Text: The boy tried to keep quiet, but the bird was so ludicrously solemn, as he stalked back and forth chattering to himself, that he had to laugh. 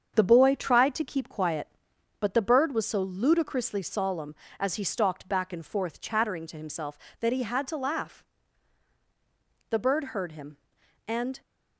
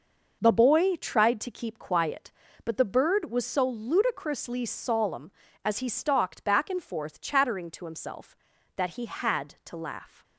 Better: second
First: starts louder than the rest; strong; until 1.1 s; 7.5 dB // goes on to say "The bird heard him and"; strong; from 9.7 s on; 1.7 s long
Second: none

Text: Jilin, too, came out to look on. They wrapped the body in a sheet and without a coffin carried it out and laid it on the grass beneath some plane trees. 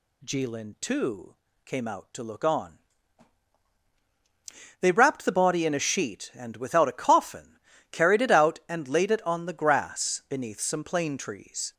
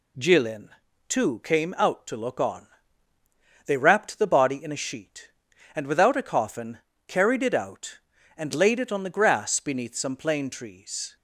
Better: neither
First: pauses between "coffin" and "carried"; slight; at 7.5 s; 0.34 s long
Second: pauses between "coffin" and "carried"; slight; at 6.7 s; 0.28 s long

